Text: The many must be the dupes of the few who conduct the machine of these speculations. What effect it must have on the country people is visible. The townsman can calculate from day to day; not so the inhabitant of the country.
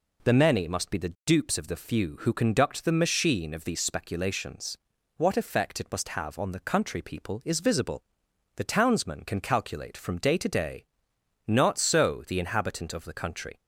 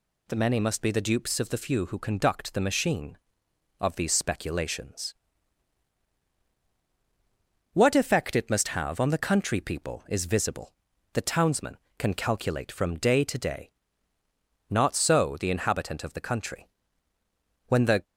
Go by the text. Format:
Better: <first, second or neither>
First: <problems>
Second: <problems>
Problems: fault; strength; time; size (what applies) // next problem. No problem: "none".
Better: first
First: none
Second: goes on to say "When the"; slight; from 17.6 s on; 0.38 s long